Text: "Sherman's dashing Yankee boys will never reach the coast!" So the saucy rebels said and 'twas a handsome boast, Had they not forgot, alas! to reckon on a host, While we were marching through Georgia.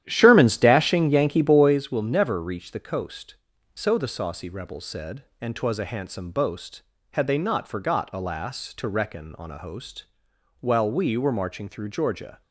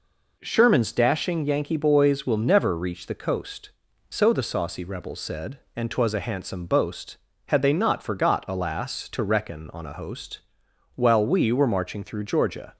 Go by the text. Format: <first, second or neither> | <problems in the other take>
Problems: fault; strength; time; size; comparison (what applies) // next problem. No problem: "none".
second | starts louder than the rest; strong; until 1.8 s; 11.5 dB